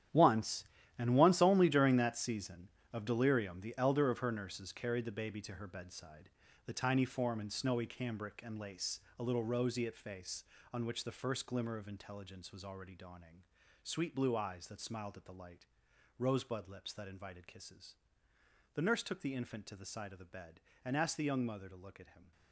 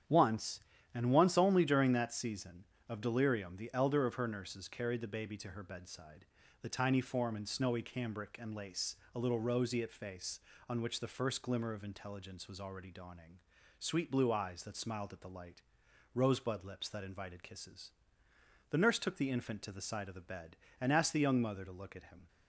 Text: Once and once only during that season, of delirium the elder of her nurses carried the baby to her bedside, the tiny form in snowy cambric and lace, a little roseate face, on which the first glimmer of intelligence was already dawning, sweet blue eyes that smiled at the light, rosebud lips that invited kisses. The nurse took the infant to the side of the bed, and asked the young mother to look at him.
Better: second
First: gets quieter; strong; throughout; 13.5 dB // starts louder than the rest; strong; until 1.4 s; 10.5 dB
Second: starts louder than the rest; strong; until 1.4 s; 9.5 dB

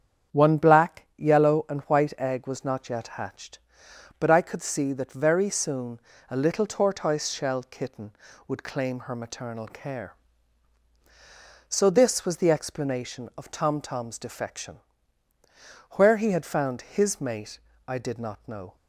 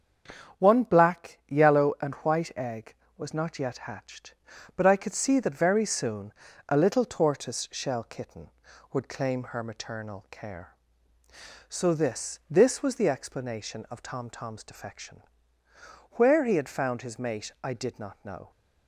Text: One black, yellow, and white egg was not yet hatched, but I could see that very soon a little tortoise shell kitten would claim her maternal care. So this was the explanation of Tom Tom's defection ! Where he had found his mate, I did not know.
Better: first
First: starts louder than the rest; strong; until 1.4 s; 8 dB // pauses between "soon" and "a"; slight; at 5.9 s; 0.30 s long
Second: starts louder than the rest; strong; until 1.6 s; 7.5 dB // pauses between "soon" and "a"; slight; at 6.3 s; 0.36 s long // says "this" twice; at 12.5 s

